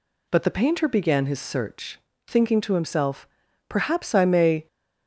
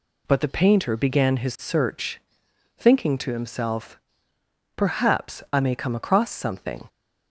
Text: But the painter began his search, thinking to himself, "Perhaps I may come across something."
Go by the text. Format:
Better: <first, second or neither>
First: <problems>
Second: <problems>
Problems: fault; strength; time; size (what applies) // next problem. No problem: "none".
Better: second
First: stops before "come across something"; at 4.6 s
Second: none